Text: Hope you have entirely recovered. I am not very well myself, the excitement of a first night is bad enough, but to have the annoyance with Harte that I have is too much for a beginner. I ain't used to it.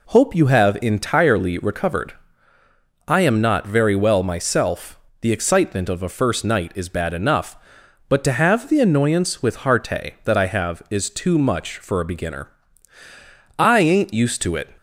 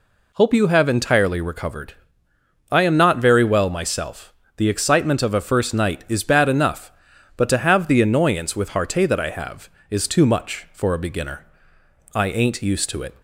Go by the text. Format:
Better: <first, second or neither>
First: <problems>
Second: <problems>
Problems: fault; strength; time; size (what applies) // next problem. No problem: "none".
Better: neither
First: none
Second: none